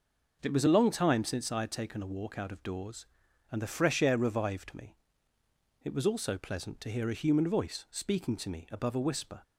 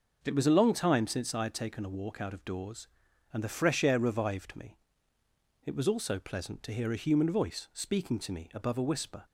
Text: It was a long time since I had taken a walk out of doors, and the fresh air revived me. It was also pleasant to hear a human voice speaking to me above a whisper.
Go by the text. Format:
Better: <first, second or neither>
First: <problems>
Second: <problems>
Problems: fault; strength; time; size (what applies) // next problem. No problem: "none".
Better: neither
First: none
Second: none